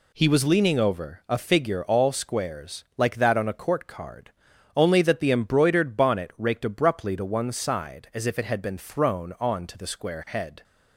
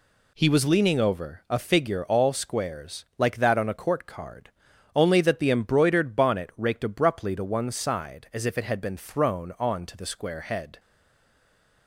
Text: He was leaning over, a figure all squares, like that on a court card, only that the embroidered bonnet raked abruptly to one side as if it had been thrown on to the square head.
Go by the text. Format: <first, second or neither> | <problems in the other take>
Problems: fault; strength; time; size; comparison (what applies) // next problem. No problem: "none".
first | stays silent after the last word; from 10.7 s on; 1.1 s long